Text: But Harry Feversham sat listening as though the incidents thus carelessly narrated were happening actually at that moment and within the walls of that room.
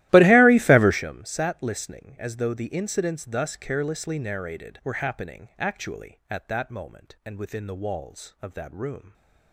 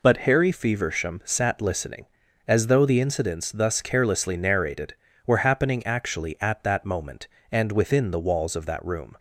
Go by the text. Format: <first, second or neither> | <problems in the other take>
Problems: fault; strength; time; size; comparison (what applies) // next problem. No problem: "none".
second | starts louder than the rest; strong; until 1.0 s; 16 dB